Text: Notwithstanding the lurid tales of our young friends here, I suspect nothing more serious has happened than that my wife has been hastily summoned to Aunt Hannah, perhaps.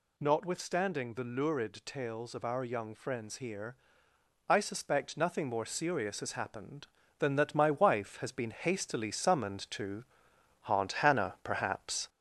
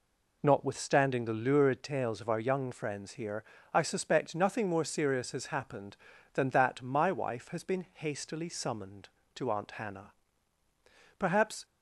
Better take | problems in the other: second | gets louder; throughout; 3.5 dB // pauses between "to" and "Aunt"; noticeable; at 10.0 s; 0.62 s long

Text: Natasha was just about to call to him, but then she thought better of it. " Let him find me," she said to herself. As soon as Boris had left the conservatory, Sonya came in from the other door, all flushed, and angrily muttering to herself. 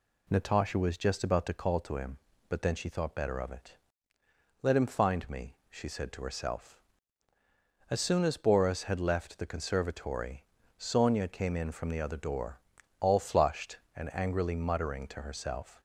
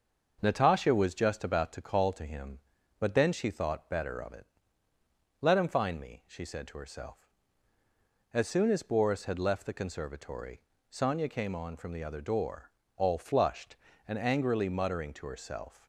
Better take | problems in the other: first | starts louder than the rest; until 1.4 s; 6.5 dB // says "on" for "in"; at 11.5 s

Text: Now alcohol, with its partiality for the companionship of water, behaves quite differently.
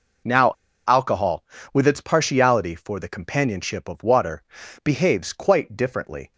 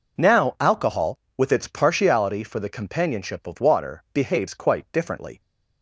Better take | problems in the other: second | pauses between "Now" and "alcohol"; at 0.5 s; 0.36 s long

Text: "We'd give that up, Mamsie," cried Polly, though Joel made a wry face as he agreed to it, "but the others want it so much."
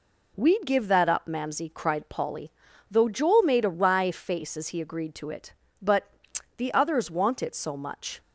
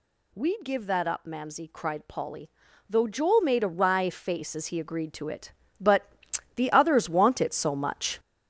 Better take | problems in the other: first | gets louder; throughout; 6.5 dB // pauses between "but" and "the"; noticeable; at 6.0 s; 0.48 s long; noticeable in the first

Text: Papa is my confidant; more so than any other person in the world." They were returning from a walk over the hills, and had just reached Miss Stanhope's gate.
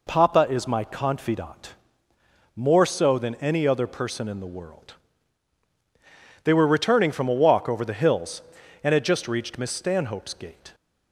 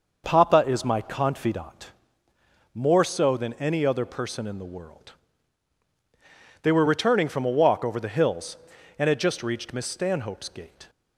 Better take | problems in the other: first | starts louder than the rest; noticeable; until 1.7 s; 6 dB

